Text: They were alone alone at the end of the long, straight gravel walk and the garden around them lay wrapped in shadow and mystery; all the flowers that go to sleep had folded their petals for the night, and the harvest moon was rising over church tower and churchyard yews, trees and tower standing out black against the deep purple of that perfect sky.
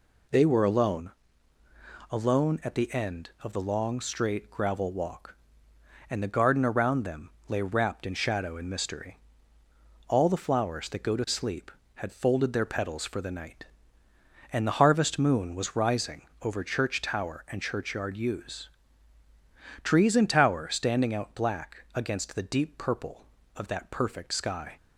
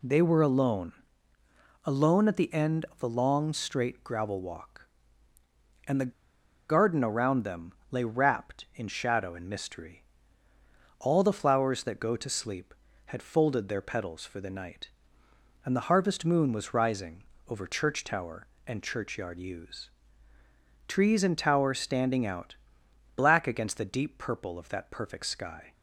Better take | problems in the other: first | pauses between "alone" and "alone"; noticeable; at 0.9 s; 0.90 s long; noticeable in the first // pauses between "the" and "garden"; noticeable; at 6.1 s; 0.56 s long // pauses between "them" and "lay"; slight; at 7.7 s; 0.18 s long; slight in the first // pauses between "rising" and "over"; slight; at 17.2 s; 0.24 s long; slight in the first // pauses between "out" and "black"; noticeable; at 22.5 s; 0.62 s long

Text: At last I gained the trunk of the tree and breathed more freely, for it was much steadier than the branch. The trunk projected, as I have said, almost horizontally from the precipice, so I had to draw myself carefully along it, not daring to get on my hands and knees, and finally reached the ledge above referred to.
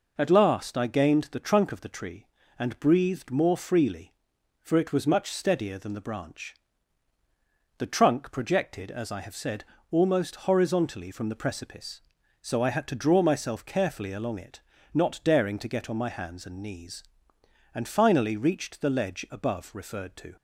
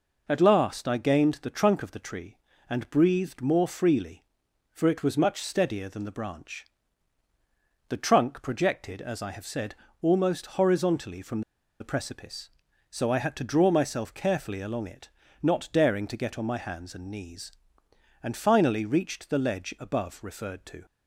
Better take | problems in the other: first | pauses between "from" and "the"; at 11.4 s; 0.39 s long

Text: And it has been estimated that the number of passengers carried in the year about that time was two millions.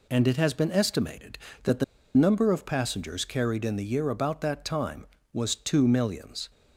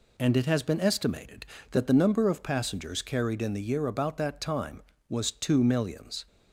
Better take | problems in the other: second | pauses between "the" and "number"; slight; at 1.8 s; 0.31 s long

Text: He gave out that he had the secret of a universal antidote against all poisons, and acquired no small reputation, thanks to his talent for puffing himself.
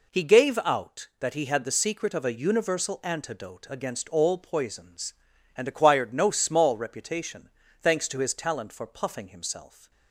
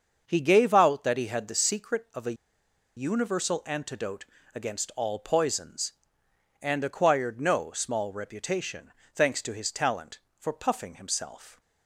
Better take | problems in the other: first | starts louder than the rest; until 1.2 s; 6.5 dB // pauses between "a" and "universal"; noticeable; at 2.3 s; 0.63 s long // pauses between "antidote" and "against"; slight; at 4.2 s; 0.30 s long

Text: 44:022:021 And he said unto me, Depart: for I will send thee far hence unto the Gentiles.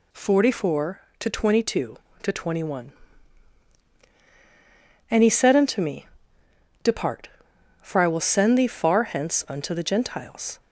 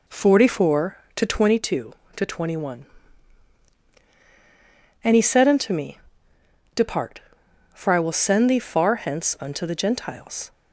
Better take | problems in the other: first | starts louder than the rest; until 1.6 s; 4 dB

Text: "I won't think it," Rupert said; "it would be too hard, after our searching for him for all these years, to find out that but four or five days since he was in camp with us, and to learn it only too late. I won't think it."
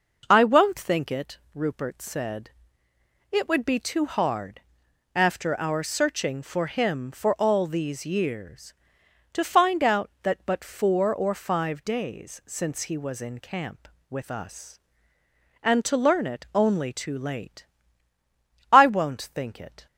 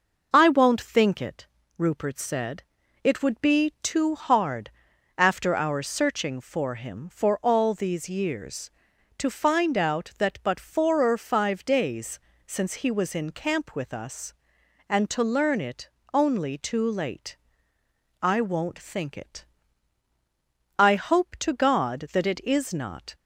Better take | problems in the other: first | pauses between "days" and "since"; slight; at 12.1 s; 0.26 s long // pauses between "it" and "only"; slight; at 15.8 s; 0.24 s long // goes on to say "I hope to God that it is not"; strong; from 20.7 s on; 2.3 s long

